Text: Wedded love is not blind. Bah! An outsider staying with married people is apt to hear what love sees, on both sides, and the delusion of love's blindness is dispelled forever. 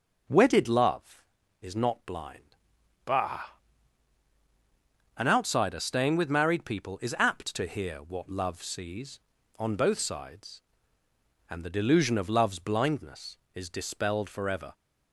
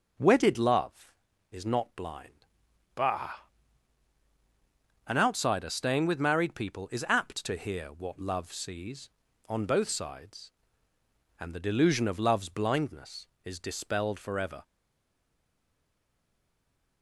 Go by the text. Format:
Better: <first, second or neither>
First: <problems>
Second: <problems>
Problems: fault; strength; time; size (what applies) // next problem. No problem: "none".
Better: first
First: none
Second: stays silent after the last word; from 14.6 s on; 2.4 s long